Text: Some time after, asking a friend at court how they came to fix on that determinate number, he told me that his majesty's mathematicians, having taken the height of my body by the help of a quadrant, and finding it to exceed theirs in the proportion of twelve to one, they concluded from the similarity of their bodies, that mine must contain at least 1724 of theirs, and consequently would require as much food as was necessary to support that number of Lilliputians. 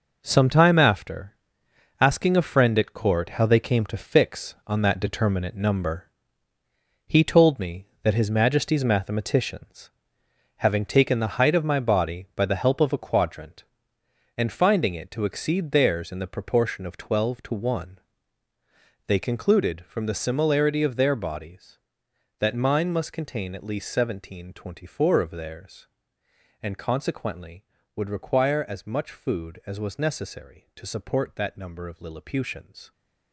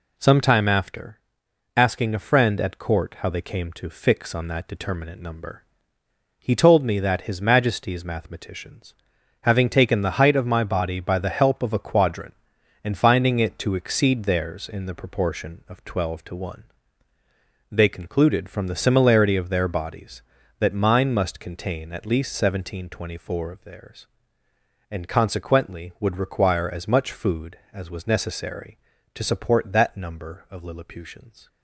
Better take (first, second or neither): second